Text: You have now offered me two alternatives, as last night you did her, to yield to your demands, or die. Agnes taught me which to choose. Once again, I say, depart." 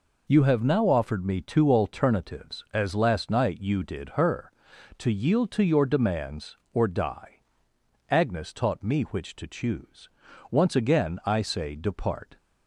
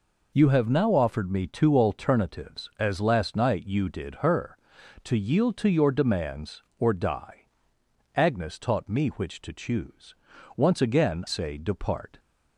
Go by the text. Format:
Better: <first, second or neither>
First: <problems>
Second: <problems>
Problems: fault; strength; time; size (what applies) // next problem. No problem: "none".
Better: first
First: none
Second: skips "I"; at 11.2 s